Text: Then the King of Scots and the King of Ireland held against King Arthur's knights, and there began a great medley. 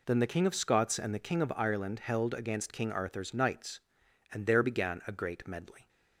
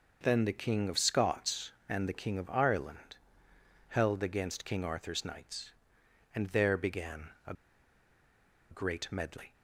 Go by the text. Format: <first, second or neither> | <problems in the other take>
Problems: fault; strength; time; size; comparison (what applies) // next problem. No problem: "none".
first | pauses between "Ireland" and "held"; noticeable; at 3.1 s; 0.72 s long // pauses between "began" and "a"; slight; at 7.2 s; 0.18 s long // pauses between "a" and "great"; at 7.5 s; 1.1 s long